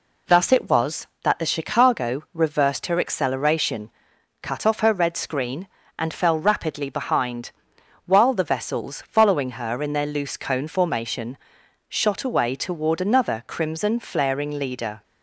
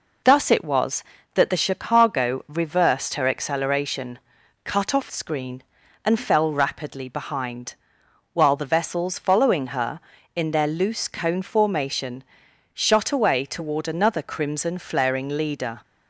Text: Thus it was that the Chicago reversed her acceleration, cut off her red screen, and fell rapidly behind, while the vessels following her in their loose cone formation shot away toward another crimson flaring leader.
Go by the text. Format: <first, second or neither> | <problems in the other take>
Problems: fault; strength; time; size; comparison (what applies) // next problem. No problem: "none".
first | skips "her red"; at 5.1 s // pauses between "formation" and "shot"; noticeable; at 12.2 s; 0.50 s long; noticeable in the first